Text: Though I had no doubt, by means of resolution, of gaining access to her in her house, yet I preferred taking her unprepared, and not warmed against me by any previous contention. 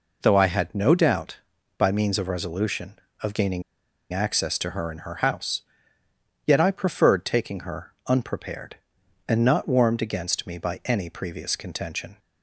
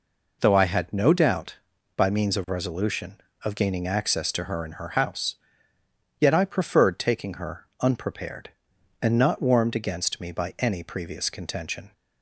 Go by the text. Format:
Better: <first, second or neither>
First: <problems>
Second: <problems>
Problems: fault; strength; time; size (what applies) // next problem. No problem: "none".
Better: second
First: pauses between "gaining" and "access"; noticeable; at 3.6 s; 0.50 s long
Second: none